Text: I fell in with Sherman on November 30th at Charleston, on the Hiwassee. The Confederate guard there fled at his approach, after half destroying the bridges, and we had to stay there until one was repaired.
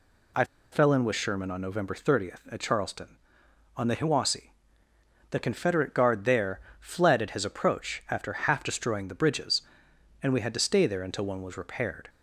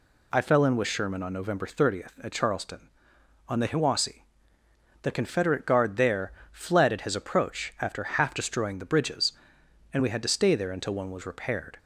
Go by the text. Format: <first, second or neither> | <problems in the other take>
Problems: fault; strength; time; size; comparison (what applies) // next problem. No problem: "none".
second | pauses between "I" and "fell"; slight; at 0.4 s; 0.28 s long // pauses between "there" and "fled"; slight; at 6.5 s; 0.22 s long; slight in the second